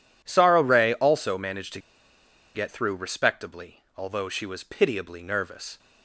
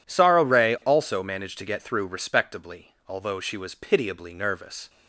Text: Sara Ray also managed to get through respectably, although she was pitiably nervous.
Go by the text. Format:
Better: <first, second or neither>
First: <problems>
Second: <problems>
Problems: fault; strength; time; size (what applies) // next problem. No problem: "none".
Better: second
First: pauses between "to" and "get"; noticeable; at 1.8 s; 0.74 s long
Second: none